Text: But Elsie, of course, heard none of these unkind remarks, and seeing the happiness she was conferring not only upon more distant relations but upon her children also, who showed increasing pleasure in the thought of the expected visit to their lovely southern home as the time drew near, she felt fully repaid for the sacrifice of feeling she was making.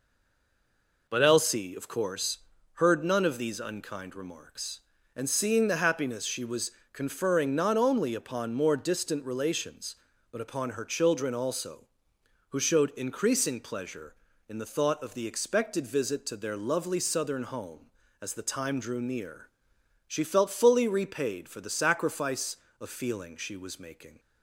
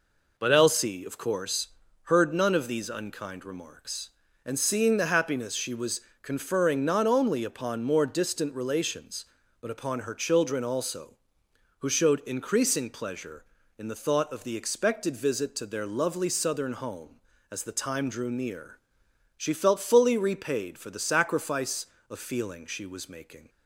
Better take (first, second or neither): second